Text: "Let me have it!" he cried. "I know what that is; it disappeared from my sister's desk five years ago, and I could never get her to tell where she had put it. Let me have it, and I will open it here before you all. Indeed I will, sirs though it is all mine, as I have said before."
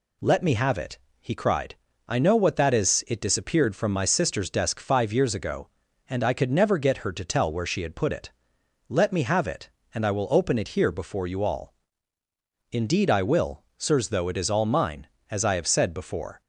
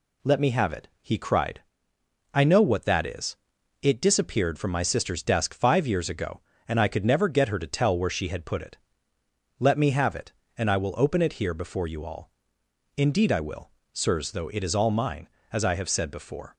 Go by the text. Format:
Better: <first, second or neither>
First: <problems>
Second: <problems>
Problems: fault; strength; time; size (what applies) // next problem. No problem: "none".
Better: neither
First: none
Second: none